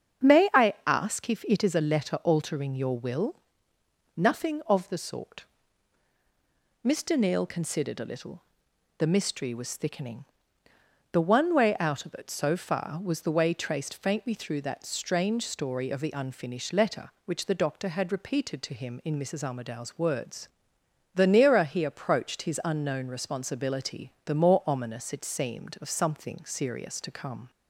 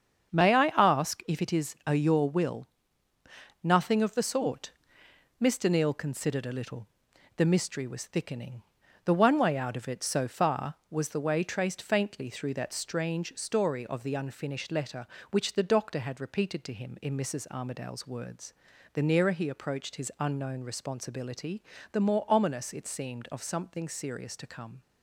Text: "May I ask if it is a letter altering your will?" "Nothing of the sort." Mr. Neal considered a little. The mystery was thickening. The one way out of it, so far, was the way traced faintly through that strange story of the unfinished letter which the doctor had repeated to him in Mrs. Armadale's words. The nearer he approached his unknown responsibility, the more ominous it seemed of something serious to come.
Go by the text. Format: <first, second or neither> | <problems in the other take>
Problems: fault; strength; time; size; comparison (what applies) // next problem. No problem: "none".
first | starts louder than the rest; strong; until 1.3 s; 7.5 dB; strong in the first // skips "letter altering"; at 1.9 s